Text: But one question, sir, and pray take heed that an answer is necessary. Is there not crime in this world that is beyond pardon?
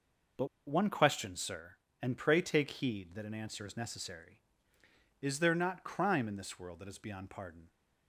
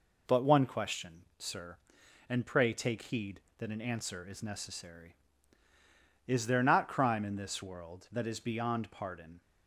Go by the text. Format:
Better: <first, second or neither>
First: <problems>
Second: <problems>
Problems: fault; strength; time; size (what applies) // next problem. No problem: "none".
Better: second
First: pauses between "But" and "one"; slight; at 0.4 s; 0.20 s long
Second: none